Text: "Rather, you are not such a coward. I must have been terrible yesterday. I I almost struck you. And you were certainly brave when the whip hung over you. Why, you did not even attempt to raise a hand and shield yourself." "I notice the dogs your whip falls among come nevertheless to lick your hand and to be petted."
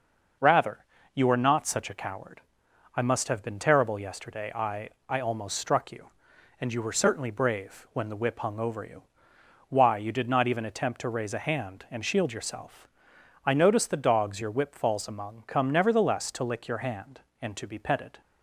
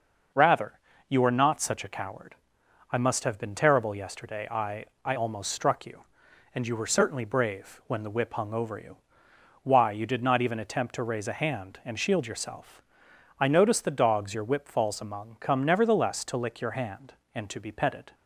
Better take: neither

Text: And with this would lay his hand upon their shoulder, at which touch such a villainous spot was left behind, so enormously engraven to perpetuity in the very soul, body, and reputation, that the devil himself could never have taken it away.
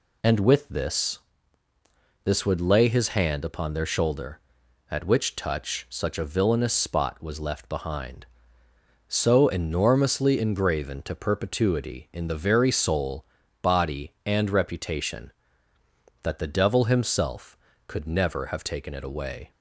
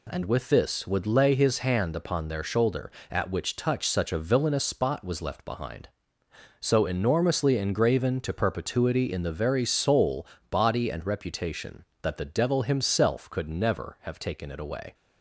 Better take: second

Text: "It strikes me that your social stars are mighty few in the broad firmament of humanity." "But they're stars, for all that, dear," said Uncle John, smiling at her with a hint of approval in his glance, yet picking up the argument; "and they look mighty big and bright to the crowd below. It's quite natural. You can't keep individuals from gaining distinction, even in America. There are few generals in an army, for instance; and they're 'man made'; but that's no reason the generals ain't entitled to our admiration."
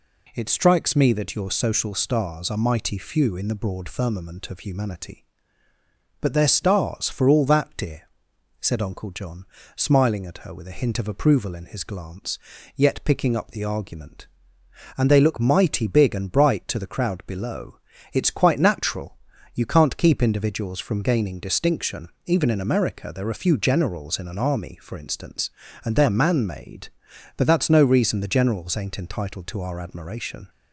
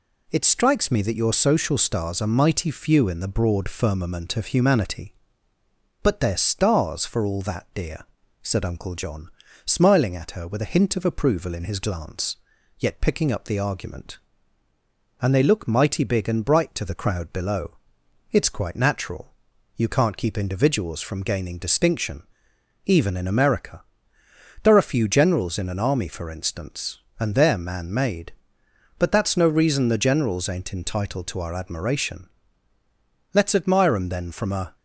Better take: first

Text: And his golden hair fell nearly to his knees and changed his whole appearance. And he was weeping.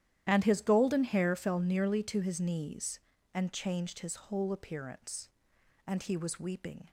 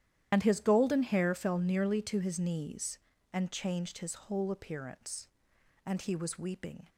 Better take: first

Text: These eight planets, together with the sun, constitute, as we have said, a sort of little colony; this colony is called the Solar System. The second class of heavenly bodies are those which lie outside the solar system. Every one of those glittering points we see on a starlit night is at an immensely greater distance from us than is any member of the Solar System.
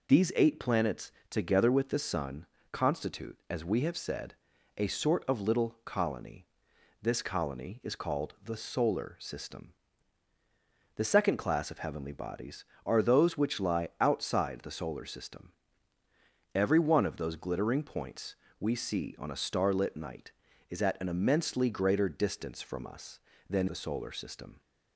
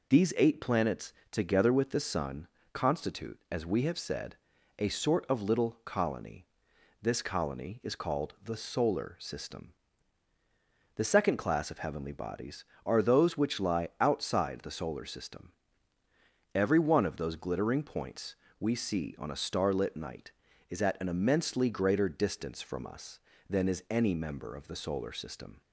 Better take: second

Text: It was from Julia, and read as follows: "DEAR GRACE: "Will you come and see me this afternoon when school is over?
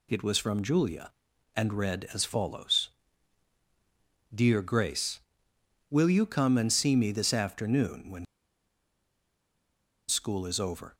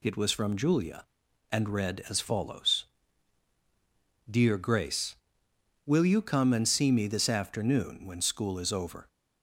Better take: second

